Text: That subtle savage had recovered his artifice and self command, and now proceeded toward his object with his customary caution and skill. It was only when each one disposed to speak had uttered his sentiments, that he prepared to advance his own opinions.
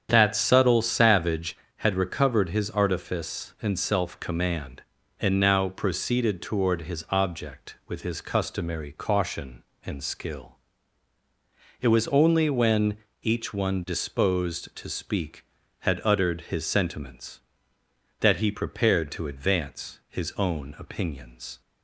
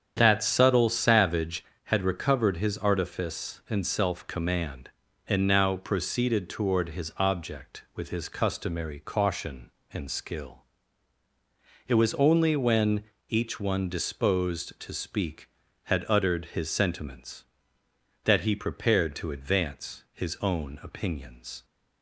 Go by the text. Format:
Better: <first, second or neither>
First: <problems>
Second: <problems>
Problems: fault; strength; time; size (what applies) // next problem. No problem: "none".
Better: neither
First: starts louder than the rest; strong; until 1.1 s; 8 dB // pauses between "when" and "each"; slight; at 12.9 s; 0.26 s long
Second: starts louder than the rest; strong; until 1.1 s; 8 dB // pauses between "when" and "each"; slight; at 13.0 s; 0.26 s long